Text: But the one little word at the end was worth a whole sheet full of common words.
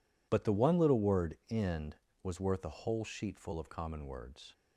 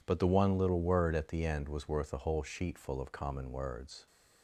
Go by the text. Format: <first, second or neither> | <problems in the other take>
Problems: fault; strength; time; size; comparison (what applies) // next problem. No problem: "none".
second | skips "at the"; at 1.4 s